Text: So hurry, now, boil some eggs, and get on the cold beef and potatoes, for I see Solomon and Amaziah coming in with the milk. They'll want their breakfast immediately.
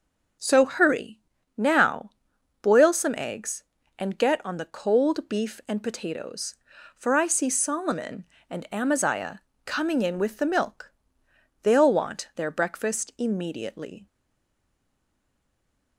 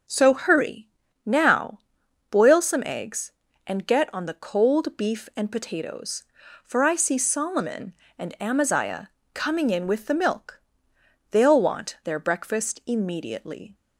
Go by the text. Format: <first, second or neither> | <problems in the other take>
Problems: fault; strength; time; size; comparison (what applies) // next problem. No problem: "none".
second | pauses between "Amaziah" and "coming"; slight; at 9.4 s; 0.24 s long; slight in the second // stays silent after the last word; noticeable; from 14.0 s on; 1.9 s long